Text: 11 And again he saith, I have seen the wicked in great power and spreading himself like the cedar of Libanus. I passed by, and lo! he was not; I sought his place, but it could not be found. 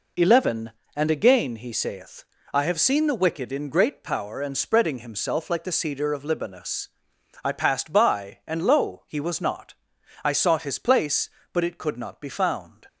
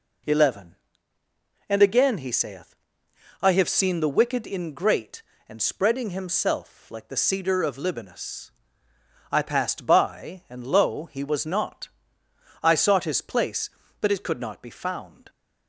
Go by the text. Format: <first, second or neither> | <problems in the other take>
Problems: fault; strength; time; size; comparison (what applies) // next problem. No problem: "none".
first | skips "power"; at 5.3 s